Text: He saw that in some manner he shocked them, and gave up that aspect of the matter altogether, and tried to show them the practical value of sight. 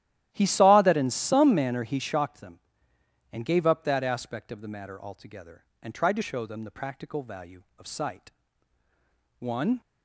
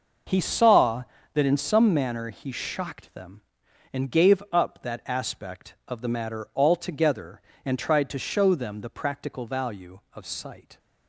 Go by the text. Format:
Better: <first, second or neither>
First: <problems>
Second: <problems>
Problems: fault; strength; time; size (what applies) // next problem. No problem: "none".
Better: second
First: starts louder than the rest; strong; until 1.3 s; 13 dB // goes on to say "One"; slight; from 9.4 s on; 0.40 s long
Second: none